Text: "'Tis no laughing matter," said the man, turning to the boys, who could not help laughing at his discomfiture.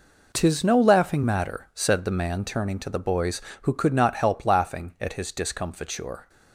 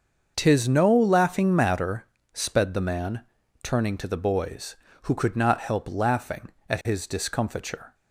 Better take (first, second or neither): first